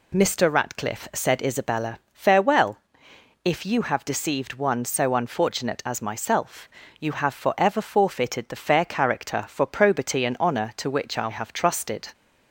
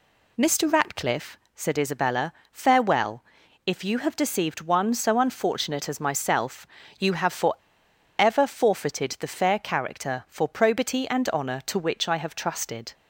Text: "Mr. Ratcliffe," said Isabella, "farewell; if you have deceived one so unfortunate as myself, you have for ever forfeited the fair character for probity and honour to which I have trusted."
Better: first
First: none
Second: pauses between "for" and "ever"; noticeable; at 7.5 s; 0.64 s long

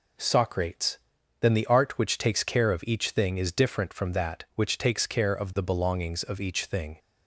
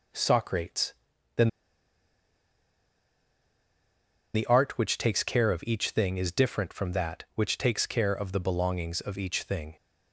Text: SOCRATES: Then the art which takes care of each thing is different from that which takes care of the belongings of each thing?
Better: first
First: none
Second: pauses between "Then" and "the"; strong; at 1.4 s; 2.8 s long

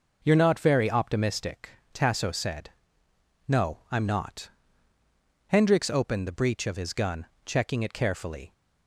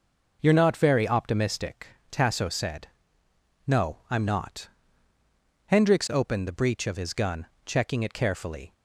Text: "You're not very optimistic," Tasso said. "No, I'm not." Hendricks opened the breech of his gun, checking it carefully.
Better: neither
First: none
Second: none

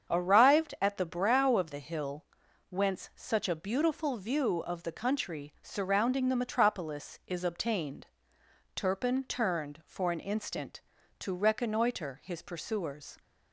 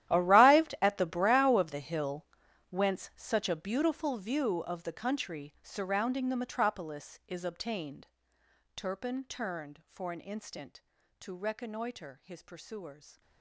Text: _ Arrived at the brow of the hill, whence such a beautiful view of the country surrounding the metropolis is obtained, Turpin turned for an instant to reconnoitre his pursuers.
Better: first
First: starts louder than the rest; strong; until 1.1 s; 7.5 dB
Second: gets quieter; strong; throughout; 18 dB // starts louder than the rest; strong; until 1.1 s; 12.5 dB

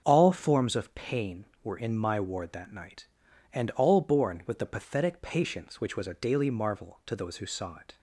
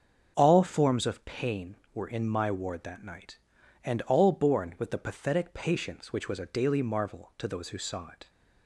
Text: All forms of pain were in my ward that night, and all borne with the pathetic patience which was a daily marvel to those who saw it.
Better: neither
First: starts louder than the rest; until 1.0 s; 6.5 dB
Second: starts louder than the rest; until 1.4 s; 6.5 dB

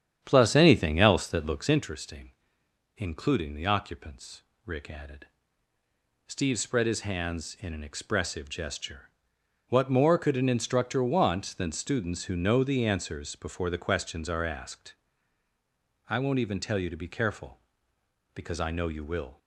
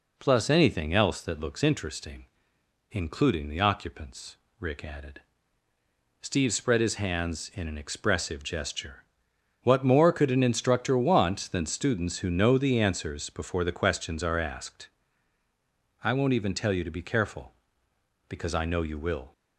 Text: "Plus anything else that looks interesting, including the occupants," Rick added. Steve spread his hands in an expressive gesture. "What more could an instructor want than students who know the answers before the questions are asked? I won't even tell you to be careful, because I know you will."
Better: second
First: starts louder than the rest; strong; until 1.9 s; 9.5 dB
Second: none

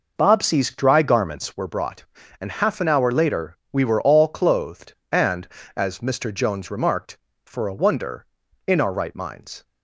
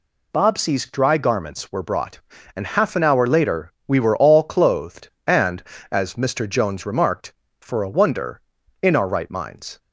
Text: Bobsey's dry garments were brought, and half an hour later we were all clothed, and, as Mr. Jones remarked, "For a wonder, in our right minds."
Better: second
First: starts louder than the rest; noticeable; until 1.7 s; 5.5 dB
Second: none

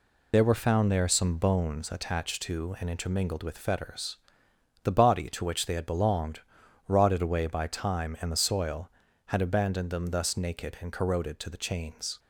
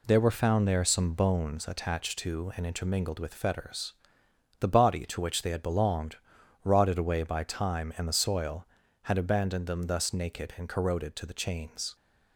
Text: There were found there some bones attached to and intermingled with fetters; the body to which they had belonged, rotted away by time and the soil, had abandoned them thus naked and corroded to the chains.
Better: second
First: loses the start of "There"; at 0.3 s; 60 ms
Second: none

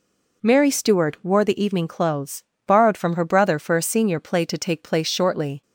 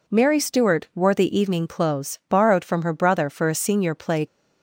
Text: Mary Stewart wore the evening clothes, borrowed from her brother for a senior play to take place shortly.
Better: first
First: none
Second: stops before "to take place shortly"; at 4.2 s

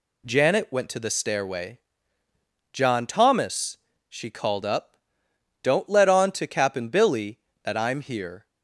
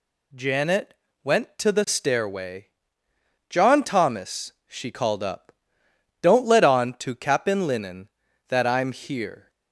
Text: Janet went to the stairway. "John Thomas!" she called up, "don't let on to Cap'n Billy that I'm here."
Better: first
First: none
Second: pauses between "Janet" and "went"; slight; at 0.9 s; 0.30 s long // says "Linen" for "Billy"; at 7.6 s

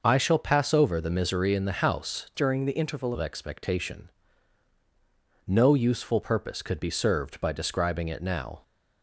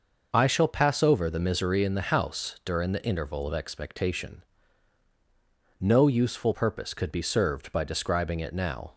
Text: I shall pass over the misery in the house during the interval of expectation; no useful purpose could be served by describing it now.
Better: second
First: changes voice from "during" to "interval"; from 2.3 to 3.1 s; 0.8 s long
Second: none

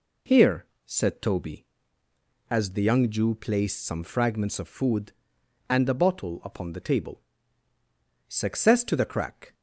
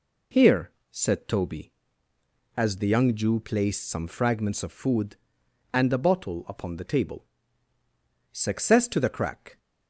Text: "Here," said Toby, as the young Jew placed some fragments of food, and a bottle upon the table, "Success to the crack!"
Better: neither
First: none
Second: none

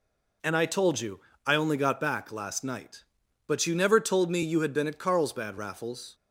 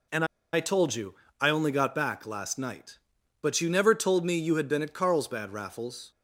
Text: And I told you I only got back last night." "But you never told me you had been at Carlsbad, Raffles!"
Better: first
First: pauses between "you" and "I"; slight; at 1.1 s; 0.26 s long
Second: pauses between "And" and "I"; slight; at 0.2 s; 0.28 s long // pauses between "you" and "I"; slight; at 1.1 s; 0.26 s long

